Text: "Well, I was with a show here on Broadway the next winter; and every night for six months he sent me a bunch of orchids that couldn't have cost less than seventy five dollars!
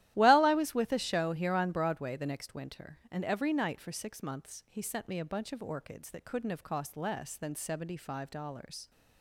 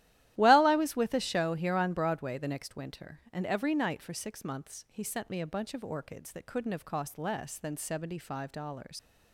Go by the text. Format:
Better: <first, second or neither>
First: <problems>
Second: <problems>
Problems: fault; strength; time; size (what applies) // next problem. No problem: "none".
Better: first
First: starts louder than the rest; strong; until 1.1 s; 14 dB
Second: starts louder than the rest; strong; until 1.3 s; 14 dB // leaves "dollars" unfinished; at 8.9 s; 125 ms